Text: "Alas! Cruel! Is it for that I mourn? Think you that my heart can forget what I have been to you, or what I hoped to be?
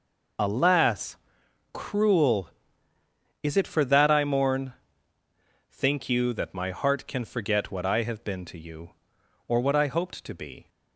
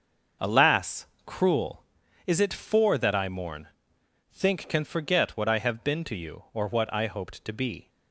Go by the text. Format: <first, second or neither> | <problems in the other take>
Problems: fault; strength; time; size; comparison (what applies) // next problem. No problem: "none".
first | starts louder than the rest; until 1.5 s; 6 dB // skips "you that my heart"; at 4.6 s